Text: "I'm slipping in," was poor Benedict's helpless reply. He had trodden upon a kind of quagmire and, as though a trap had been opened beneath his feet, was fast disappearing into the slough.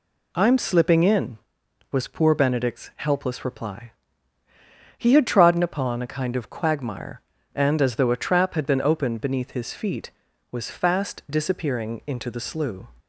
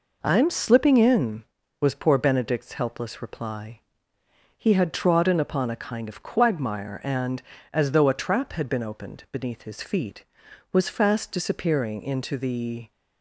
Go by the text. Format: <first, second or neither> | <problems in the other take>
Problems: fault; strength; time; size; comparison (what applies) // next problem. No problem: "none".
first | stops before "slough"; at 12.9 s